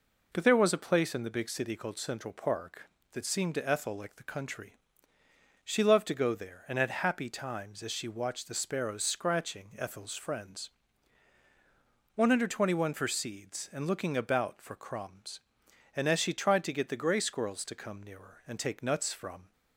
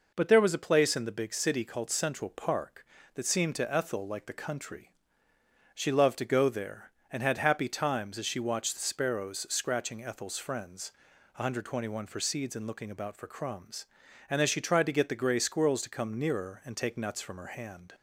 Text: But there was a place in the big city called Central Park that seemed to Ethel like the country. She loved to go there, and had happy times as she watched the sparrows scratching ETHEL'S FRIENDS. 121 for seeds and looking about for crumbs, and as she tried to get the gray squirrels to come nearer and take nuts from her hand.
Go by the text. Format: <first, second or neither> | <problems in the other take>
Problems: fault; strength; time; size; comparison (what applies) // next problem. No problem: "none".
second | stops before "her hand"; at 19.5 s